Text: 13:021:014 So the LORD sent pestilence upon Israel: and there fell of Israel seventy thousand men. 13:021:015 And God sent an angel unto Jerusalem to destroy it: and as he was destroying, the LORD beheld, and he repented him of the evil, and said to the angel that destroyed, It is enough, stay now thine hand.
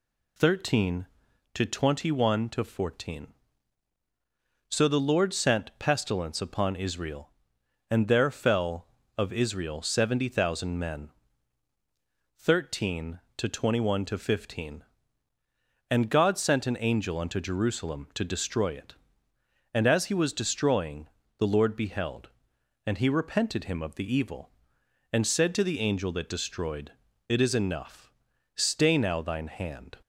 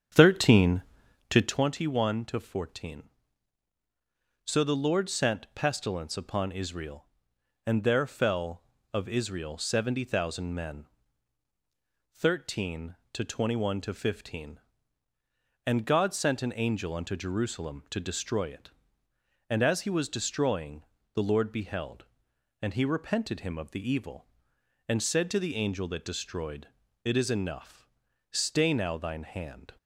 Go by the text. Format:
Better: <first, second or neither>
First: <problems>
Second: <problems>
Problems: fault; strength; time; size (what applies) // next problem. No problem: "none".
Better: first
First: none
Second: starts louder than the rest; strong; until 1.6 s; 8 dB